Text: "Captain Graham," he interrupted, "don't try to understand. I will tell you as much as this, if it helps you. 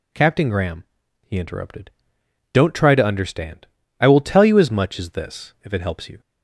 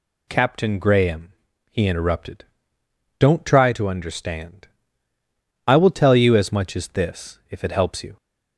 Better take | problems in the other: neither | none

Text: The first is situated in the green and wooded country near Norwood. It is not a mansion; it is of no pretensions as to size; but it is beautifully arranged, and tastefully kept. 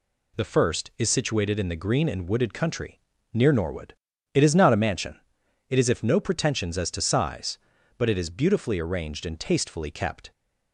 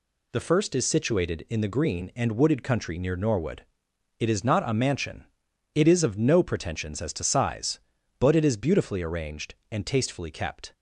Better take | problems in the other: second | pauses between "country" and "near"; slight; at 2.9 s; 0.34 s long // says "if" for "of"; at 5.8 s

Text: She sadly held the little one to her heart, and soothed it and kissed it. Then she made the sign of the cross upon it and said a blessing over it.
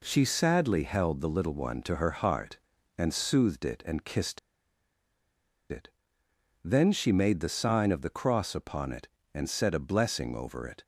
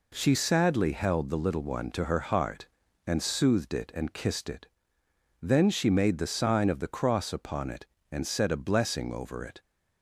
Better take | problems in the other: second | pauses between "kissed" and "it"; strong; at 4.3 s; 1.3 s long

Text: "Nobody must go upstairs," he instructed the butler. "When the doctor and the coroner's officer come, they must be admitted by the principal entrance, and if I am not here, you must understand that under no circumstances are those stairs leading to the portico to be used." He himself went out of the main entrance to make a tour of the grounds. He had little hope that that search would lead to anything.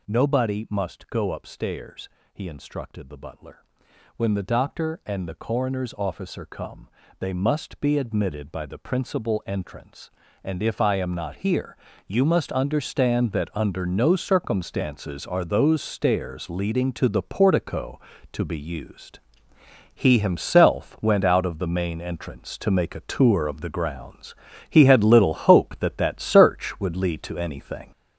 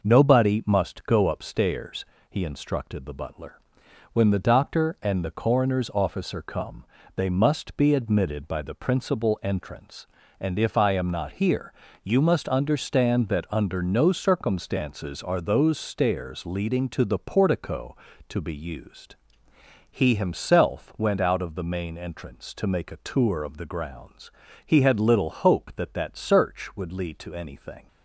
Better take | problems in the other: second | gets louder; noticeable; throughout; 6 dB

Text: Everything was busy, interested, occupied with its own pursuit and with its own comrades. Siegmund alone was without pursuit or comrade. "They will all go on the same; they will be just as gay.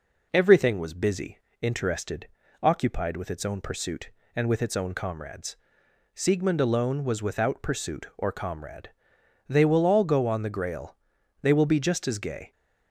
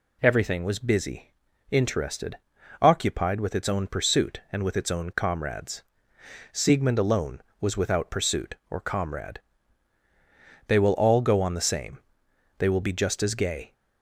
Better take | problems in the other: second | says "grail" for "same"; at 10.4 s

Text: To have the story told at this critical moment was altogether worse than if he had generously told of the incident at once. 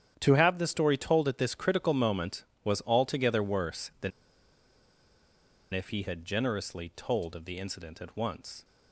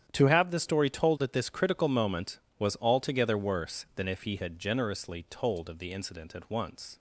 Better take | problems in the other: second | starts louder than the rest; strong; until 1.2 s; 10 dB; strong in the second // pauses between "than" and "if"; strong; at 4.1 s; 1.6 s long

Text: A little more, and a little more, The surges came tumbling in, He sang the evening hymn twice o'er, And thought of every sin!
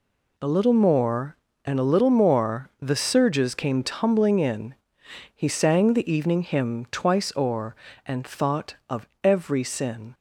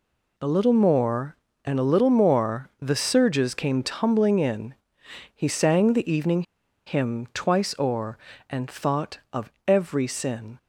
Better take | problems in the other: first | pauses between "evening" and "hymn"; at 6.4 s; 0.43 s long // pauses between "of" and "every"; slight; at 9.4 s; 0.16 s long; slight in the first

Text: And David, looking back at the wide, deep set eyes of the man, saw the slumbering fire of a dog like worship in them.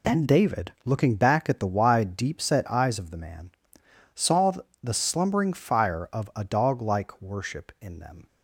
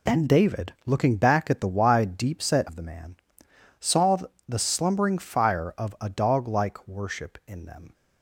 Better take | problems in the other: first | skips "eyes"; at 2.6 s // pauses between "saw" and "the"; slight; at 4.1 s; 0.30 s long; slight in the first

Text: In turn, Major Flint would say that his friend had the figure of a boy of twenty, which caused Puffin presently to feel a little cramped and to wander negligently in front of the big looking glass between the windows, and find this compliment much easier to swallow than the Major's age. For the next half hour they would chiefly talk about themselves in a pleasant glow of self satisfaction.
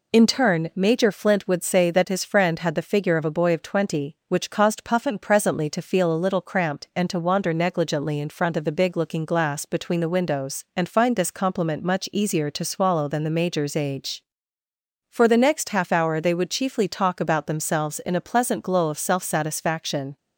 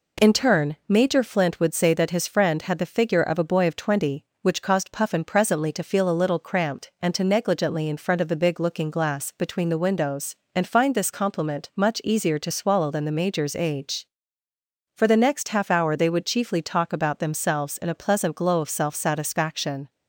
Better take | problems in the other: first | skips "wander"; at 7.2 s

